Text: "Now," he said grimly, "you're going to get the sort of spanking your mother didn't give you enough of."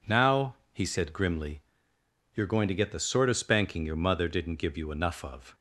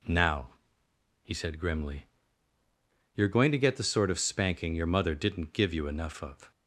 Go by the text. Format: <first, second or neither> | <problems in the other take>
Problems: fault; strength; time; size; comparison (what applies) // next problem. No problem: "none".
neither | none